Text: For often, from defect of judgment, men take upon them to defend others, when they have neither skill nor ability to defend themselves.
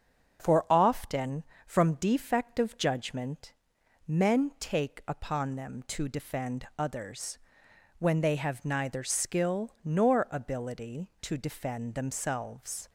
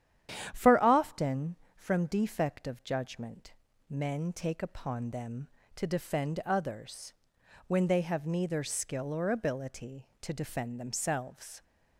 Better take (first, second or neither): first